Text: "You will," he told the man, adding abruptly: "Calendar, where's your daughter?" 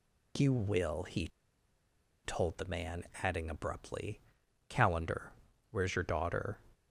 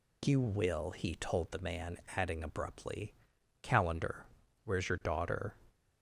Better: second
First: pauses between "he" and "told"; noticeable; at 1.2 s; 0.96 s long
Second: none

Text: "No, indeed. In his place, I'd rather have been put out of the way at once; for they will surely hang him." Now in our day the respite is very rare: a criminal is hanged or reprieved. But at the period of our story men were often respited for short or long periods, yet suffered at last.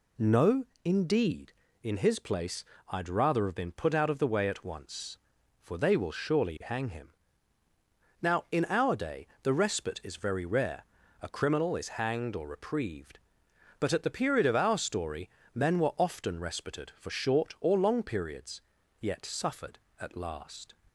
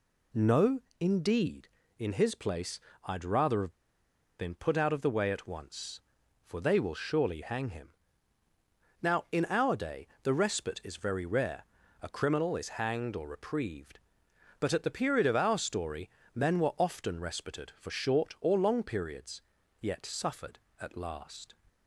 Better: first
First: pauses between "story" and "men"; slight; at 15.2 s; 0.26 s long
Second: pauses between "have" and "been"; noticeable; at 3.6 s; 0.69 s long // pauses between "story" and "men"; slight; at 16.0 s; 0.26 s long

